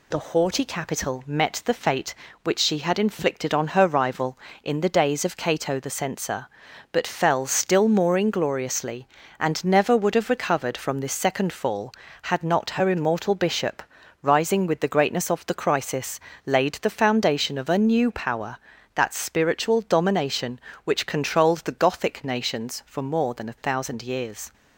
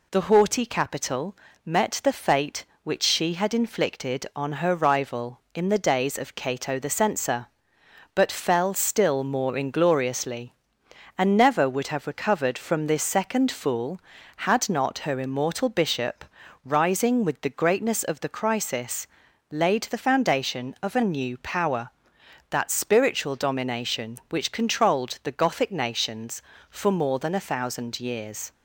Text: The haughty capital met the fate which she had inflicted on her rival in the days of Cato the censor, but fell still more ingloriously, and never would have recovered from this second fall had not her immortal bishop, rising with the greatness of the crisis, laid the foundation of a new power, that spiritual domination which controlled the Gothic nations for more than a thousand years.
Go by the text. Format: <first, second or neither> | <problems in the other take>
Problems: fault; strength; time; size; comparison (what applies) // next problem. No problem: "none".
first | pauses between "capital" and "met"; slight; at 1.3 s; 0.30 s long // says "fool" for "fall"; at 13.5 s